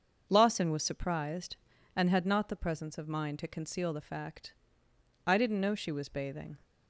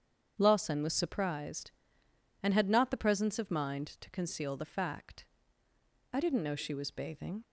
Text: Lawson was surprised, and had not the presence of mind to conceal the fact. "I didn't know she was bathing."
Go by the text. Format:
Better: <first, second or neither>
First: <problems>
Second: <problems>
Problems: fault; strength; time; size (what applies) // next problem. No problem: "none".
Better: neither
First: starts louder than the rest; until 1.3 s; 6.5 dB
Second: starts louder than the rest; strong; until 1.3 s; 8 dB